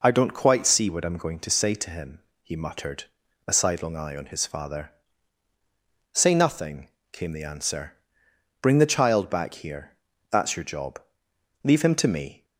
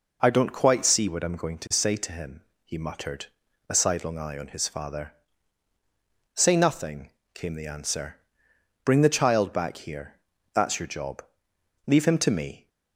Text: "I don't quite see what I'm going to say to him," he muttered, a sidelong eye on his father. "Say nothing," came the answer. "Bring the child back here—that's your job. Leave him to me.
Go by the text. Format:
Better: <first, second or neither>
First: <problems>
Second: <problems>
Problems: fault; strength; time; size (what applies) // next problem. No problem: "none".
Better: neither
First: none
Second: none